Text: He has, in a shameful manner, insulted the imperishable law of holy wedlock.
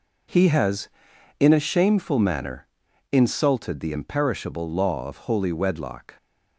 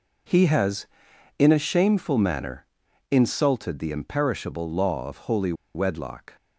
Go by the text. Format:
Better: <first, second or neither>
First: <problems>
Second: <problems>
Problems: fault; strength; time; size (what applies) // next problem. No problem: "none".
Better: first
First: none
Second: pauses between "holy" and "wedlock"; slight; at 5.5 s; 0.21 s long